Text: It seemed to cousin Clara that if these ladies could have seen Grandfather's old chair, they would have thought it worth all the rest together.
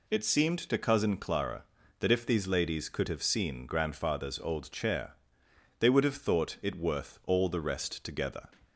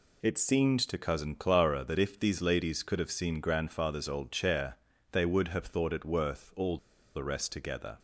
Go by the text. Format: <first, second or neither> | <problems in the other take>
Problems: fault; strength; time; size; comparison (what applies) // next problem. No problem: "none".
first | pauses between "all" and "the"; at 6.7 s; 0.37 s long